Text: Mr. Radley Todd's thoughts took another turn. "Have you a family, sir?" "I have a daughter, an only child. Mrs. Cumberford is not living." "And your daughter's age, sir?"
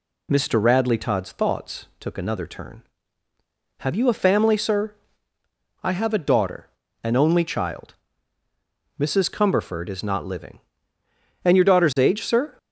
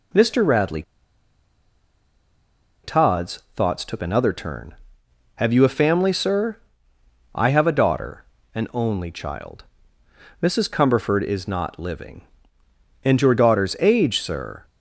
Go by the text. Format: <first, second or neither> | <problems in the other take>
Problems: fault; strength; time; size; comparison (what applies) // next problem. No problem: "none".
first | pauses between "Radley" and "Todd's"; strong; at 0.8 s; 2.0 s long